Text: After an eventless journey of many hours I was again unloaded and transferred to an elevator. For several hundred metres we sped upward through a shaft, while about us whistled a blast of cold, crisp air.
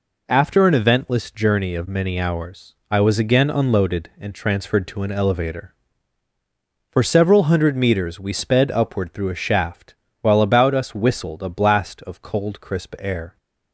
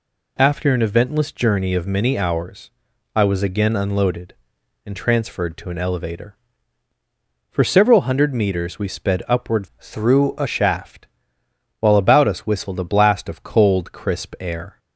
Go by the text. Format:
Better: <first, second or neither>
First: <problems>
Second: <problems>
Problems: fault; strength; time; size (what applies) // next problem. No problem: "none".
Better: first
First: pauses between "hours" and "I"; slight; at 2.7 s; 0.16 s long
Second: pauses between "hours" and "I"; noticeable; at 2.6 s; 0.46 s long // changes voice from "through" to "a"; from 9.7 to 10.4 s; 0.7 s long